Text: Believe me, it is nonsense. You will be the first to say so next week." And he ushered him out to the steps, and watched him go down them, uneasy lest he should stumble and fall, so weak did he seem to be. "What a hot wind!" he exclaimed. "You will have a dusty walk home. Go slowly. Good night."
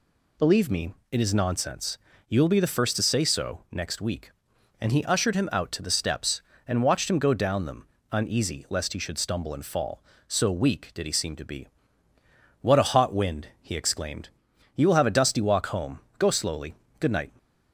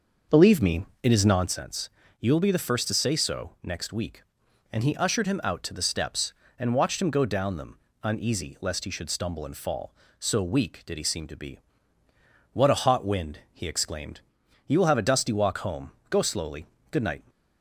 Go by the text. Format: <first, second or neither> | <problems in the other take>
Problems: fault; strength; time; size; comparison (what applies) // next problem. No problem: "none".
first | starts louder than the rest; until 1.5 s; 6 dB